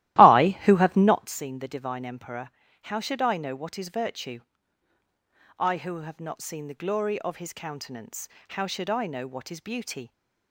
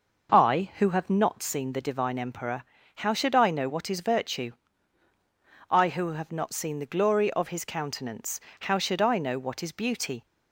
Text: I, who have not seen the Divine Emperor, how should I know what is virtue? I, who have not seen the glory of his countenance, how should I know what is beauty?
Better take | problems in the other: second | starts louder than the rest; strong; until 1.4 s; 15 dB

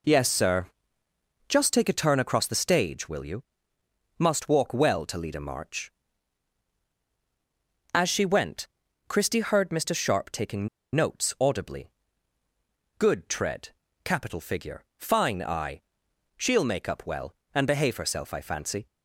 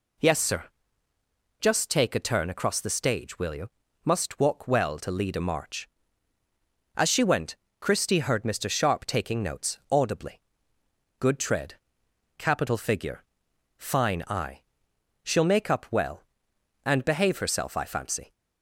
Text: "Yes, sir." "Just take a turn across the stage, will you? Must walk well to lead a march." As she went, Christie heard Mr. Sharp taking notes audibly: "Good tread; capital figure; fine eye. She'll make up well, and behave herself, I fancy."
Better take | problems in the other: second | pauses between "taking" and "notes"; slight; at 10.6 s; 0.27 s long

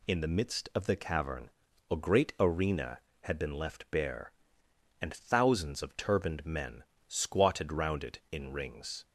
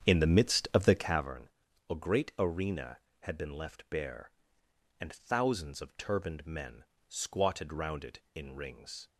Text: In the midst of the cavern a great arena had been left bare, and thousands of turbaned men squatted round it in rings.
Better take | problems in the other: first | starts louder than the rest; strong; until 1.3 s; 8.5 dB // pauses between "cavern" and "a"; at 1.4 s; 0.40 s long; also in the first // pauses between "men" and "squatted"; slight; at 6.8 s; 0.22 s long; slight in the first

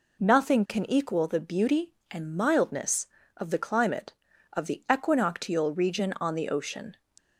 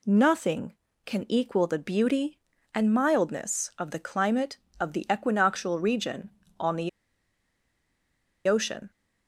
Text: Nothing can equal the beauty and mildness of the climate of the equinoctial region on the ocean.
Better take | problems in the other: first | pauses between "the" and "ocean"; strong; at 6.8 s; 1.5 s long

